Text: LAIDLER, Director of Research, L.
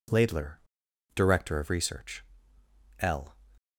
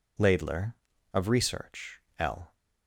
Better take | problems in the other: first | skips "Director"; at 0.9 s

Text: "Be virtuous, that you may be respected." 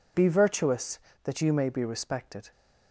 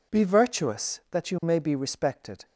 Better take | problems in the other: neither | none

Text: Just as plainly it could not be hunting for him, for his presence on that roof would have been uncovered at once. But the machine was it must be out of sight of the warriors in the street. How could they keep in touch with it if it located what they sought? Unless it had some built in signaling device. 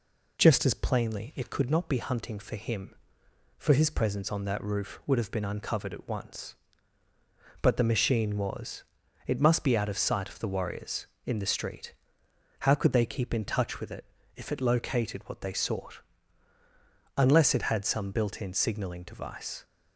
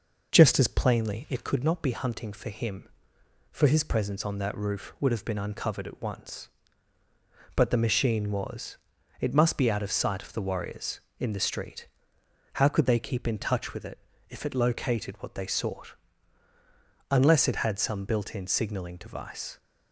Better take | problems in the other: first | starts louder than the rest; noticeable; until 1.5 s; 5.5 dB // pauses between "was" and "it"; at 8.7 s; 0.42 s long; also in the first // pauses between "it" and "if"; slight; at 13.9 s; 0.30 s long; slight in the first

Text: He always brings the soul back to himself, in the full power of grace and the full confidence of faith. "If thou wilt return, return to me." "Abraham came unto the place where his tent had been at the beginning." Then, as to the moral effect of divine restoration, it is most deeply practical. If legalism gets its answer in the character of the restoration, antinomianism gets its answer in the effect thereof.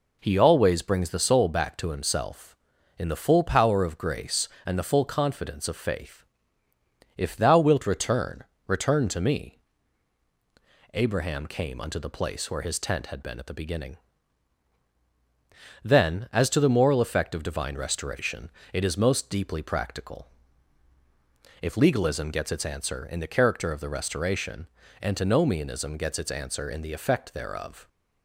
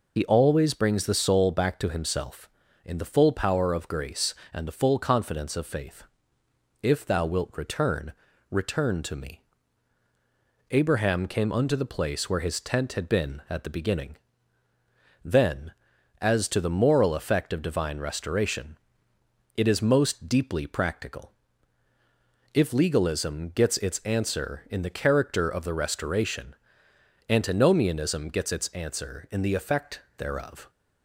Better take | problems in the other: first | loses the start of "He"; at 0.1 s; 65 ms // pauses between "effect" and "thereof"; slight; at 29.9 s; 0.18 s long

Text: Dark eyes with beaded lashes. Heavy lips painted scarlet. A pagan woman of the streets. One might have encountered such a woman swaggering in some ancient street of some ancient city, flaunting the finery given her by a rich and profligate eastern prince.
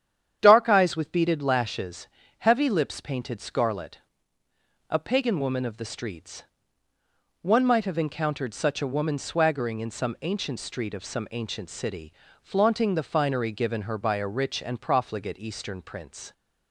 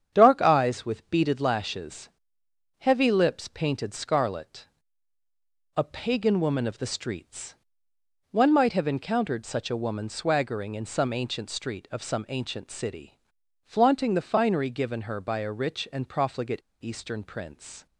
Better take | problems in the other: first | starts louder than the rest; strong; until 1.1 s; 8.5 dB; strong in the first // pauses between "profligate" and "eastern"; slight; at 16.6 s; 0.21 s long

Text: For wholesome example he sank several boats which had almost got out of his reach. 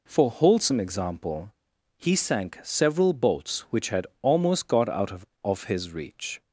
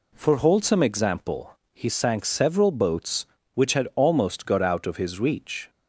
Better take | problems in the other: second | pauses between "example" and "he"; noticeable; at 1.5 s; 0.48 s long; slight in the second // says "of" twice; at 5.4 s

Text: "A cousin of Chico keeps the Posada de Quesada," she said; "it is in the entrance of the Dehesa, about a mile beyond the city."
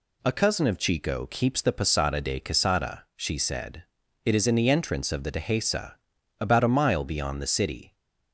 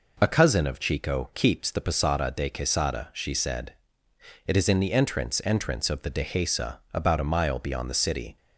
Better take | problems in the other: first | says "entrance" twice; at 5.4 s

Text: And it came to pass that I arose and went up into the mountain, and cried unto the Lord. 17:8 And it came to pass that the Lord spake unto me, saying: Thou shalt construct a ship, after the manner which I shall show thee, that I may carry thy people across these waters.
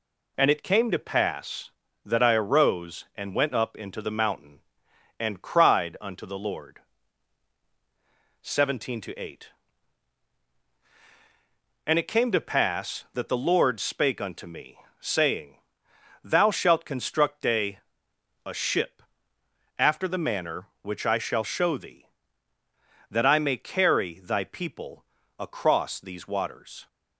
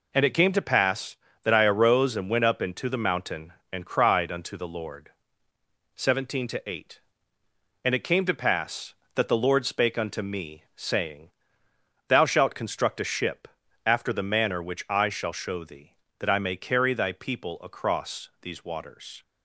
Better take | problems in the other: second | says "a" twice; at 18.4 s // pauses between "people" and "across"; slight; at 25.0 s; 0.34 s long

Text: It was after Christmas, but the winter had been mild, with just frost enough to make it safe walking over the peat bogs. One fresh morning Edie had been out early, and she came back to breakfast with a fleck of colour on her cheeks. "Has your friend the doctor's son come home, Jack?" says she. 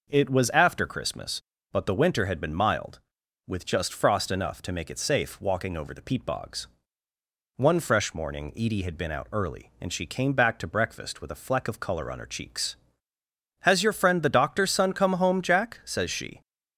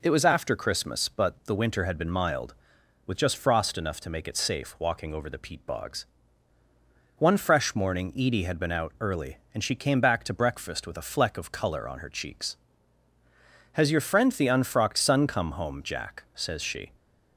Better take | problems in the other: first | says "unfrocked" for "doctor's"; at 14.4 s

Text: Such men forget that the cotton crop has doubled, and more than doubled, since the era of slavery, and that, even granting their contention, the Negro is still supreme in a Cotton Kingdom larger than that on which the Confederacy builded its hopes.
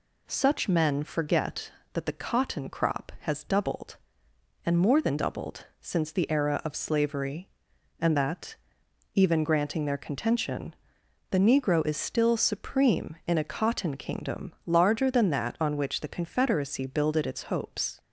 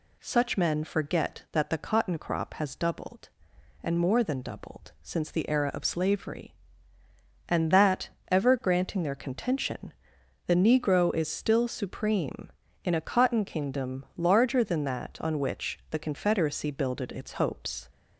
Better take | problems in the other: first | says "ever" for "even"; at 8.2 s

